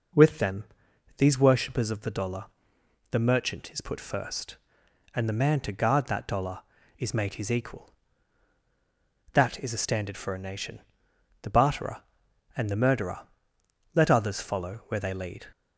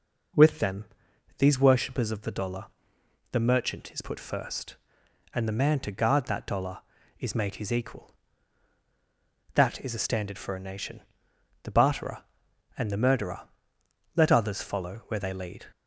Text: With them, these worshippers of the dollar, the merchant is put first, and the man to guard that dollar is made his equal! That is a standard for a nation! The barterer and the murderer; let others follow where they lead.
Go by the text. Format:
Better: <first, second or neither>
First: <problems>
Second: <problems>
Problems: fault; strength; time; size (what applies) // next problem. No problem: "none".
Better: neither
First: none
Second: none